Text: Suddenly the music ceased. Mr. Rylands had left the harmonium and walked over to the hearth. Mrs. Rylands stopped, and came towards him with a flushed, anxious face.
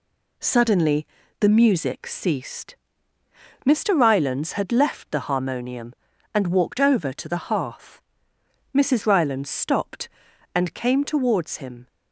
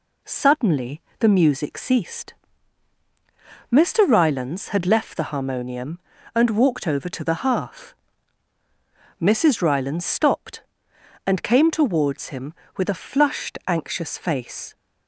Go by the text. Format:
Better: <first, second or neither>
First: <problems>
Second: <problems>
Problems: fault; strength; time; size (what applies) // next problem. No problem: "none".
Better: second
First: pauses between "Suddenly" and "the"; slight; at 1.0 s; 0.34 s long // stops before "with a flushed anxious face"; at 11.8 s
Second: pauses between "Suddenly" and "the"; slight; at 1.0 s; 0.18 s long